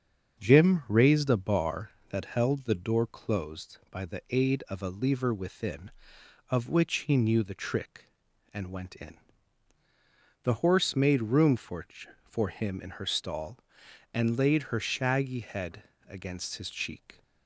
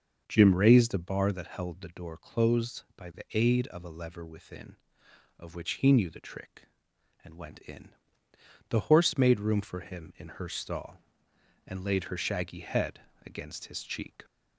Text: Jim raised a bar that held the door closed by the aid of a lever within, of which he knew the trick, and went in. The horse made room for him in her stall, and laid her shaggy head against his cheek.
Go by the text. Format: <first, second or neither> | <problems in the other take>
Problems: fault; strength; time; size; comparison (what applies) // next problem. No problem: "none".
second | starts louder than the rest; until 1.4 s; 6.5 dB; also in the second // says "for" twice; at 12.2 s // pauses between "head" and "against"; slight; at 15.8 s; 0.22 s long; slight in the second